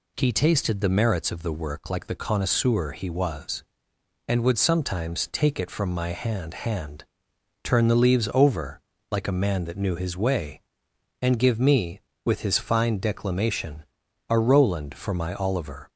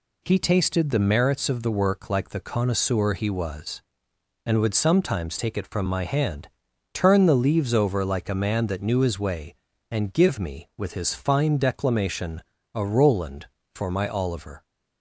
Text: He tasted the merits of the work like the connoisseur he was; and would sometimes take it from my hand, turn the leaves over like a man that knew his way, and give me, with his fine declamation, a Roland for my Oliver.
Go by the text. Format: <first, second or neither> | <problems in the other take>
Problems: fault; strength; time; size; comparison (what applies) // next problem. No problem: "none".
second | says "hand" twice; at 6.5 s // pauses between "over" and "like"; slight; at 8.8 s; 0.28 s long